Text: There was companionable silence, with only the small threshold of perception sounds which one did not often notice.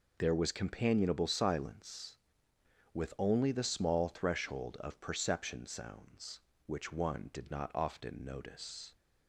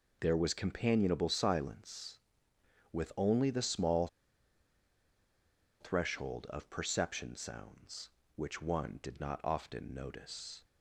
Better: first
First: none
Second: pauses between "small" and "threshold"; strong; at 4.0 s; 1.7 s long

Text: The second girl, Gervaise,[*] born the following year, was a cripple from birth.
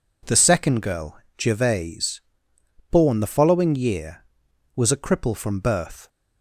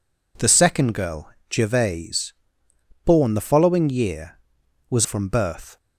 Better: first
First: none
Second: skips "a cripple"; at 5.0 s

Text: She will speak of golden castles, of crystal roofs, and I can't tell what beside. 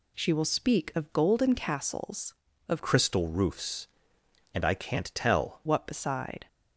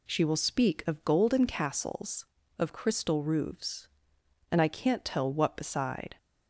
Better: second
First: changes voice from "crystal" to "tell"; from 2.8 to 5.6 s; 2.8 s long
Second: none

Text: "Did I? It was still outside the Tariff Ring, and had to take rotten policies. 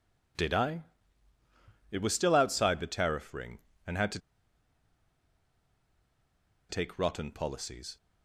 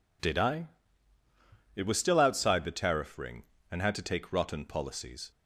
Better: second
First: pauses between "to" and "take"; strong; at 4.1 s; 2.5 s long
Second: none

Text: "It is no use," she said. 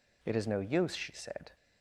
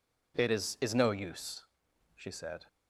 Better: first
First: none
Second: says "is" twice; at 0.8 s

